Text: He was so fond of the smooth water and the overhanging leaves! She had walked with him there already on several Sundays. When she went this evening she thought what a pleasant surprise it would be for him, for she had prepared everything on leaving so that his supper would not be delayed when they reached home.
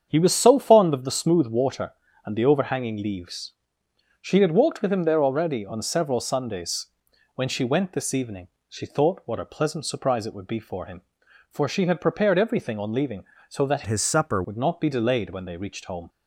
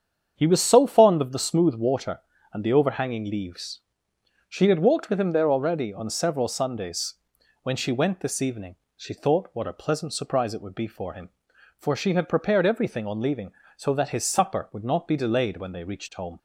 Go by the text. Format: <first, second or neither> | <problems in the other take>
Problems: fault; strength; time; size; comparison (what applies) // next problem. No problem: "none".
second | starts louder than the rest; strong; until 1.1 s; 8 dB; strong in the second // pauses between "evening" and "she"; slight; at 8.4 s; 0.22 s long; slight in the second // changes voice from "his" to "supper"; from 13.8 to 14.4 s; 0.6 s long